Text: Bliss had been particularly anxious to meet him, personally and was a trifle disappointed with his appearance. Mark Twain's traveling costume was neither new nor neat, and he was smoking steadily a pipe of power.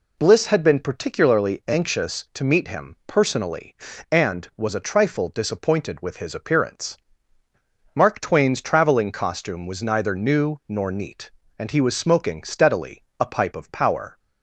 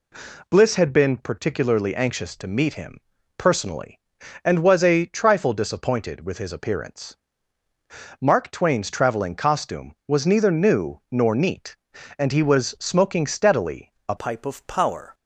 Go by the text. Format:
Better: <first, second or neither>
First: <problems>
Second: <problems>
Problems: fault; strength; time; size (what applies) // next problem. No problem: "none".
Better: first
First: pauses between "steadily" and "a"; slight; at 13.0 s; 0.18 s long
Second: pauses between "steadily" and "a"; slight; at 13.9 s; 0.16 s long // changes voice at "pipe"; from 14.1 s on; 1.0 s long